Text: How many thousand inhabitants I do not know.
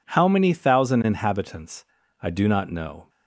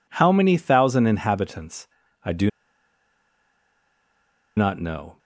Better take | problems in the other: first | pauses between "inhabitants" and "I"; slight; at 1.8 s; 0.36 s long; slight in the first // pauses between "do" and "not"; strong; at 2.4 s; 2.0 s long

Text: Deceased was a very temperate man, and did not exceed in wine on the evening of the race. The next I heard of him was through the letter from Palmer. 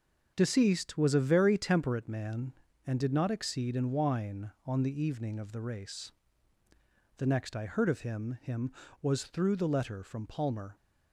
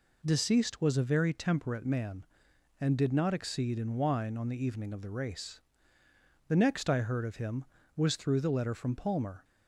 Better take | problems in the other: second | starts louder than the rest; until 1.3 s; 6.5 dB // says "him" twice; at 8.4 s

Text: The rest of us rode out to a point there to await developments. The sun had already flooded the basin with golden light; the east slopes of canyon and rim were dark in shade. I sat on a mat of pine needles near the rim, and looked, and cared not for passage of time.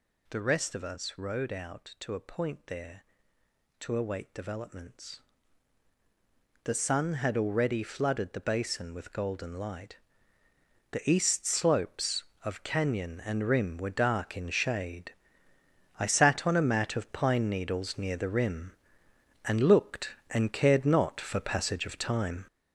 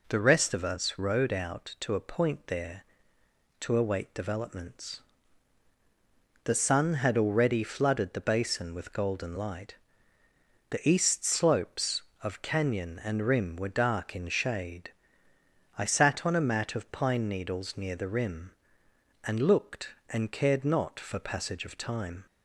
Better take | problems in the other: second | gets louder; strong; throughout; 7.5 dB

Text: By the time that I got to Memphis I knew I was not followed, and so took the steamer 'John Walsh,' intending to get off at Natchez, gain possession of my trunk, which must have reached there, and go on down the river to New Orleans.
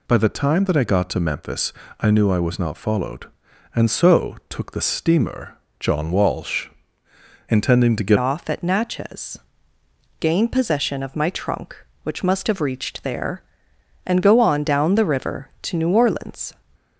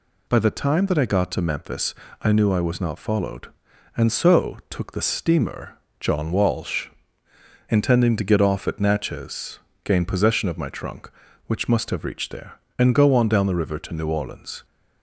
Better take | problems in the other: second | pauses between "Memphis" and "I"; slight; at 1.7 s; 0.26 s long; slight in the second // pauses between "steamer" and "John"; slight; at 5.5 s; 0.24 s long; slight in the second // changes voice at "off"; from 8.1 s on; 8.4 s long

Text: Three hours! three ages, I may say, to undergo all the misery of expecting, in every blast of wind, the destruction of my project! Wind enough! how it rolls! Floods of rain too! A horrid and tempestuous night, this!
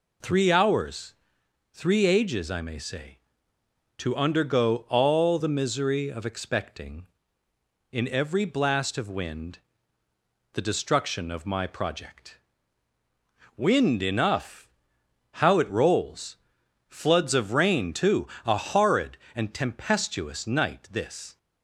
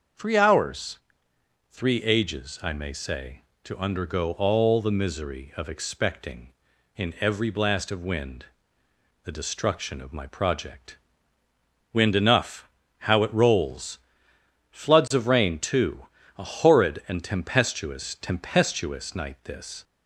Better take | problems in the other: first | starts louder than the rest; until 1.8 s; 6.5 dB // says "tempestuous" twice; at 18.1 s

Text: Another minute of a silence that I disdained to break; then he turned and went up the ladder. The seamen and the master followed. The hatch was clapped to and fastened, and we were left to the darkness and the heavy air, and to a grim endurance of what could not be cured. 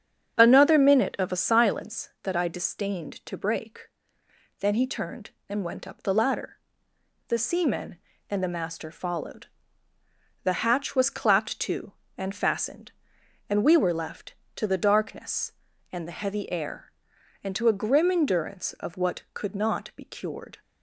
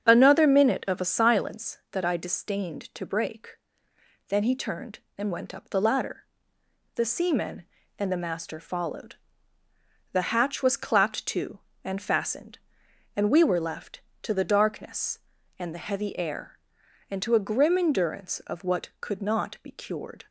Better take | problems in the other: neither | starts louder than the rest; strong; the same in both

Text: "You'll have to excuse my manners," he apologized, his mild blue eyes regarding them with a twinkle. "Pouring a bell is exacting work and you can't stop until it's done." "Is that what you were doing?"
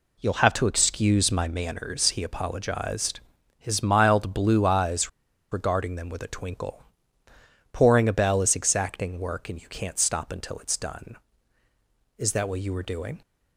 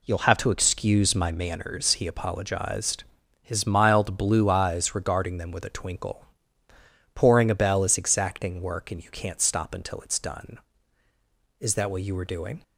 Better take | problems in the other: second | pauses between "eyes" and "regarding"; at 5.0 s; 0.43 s long

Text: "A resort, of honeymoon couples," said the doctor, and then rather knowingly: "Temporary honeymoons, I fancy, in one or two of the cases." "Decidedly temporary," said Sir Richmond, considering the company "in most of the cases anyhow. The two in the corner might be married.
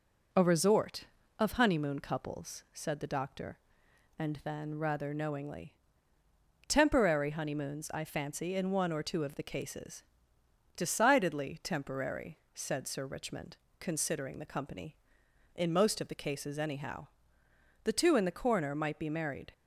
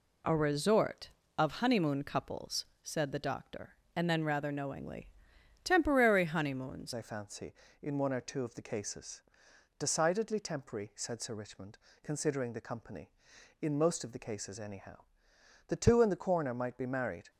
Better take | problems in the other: first | changes voice at "I"; from 6.9 s on; 10.4 s long

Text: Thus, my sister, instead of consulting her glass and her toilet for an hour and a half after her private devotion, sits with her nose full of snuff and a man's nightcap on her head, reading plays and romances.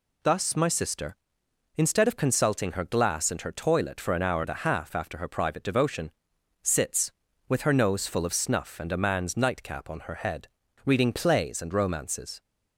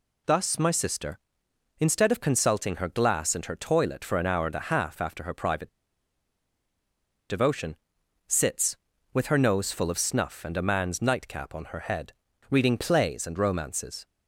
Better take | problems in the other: first | pauses between "private" and "devotion"; strong; at 5.6 s; 1.6 s long

